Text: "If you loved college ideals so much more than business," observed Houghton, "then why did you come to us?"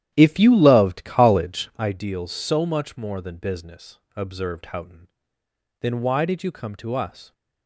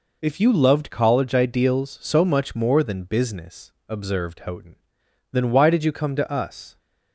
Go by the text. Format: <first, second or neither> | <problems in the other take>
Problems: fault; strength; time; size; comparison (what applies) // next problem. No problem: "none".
second | starts louder than the rest; strong; until 1.9 s; 11.5 dB